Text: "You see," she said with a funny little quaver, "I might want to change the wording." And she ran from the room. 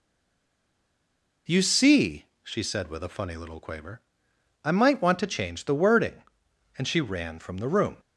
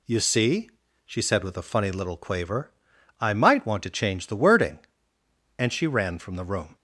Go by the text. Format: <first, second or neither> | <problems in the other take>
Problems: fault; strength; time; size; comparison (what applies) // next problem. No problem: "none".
second | stays silent before the first word; noticeable; until 1.4 s; 1.4 s long